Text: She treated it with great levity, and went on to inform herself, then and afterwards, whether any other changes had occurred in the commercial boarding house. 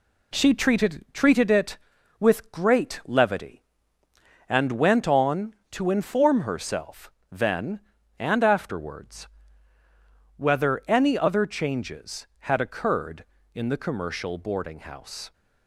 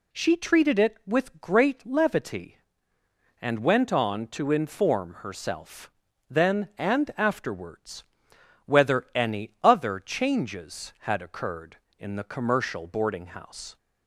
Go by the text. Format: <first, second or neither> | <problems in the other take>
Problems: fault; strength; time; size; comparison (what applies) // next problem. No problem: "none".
second | says "treated" twice; at 1.1 s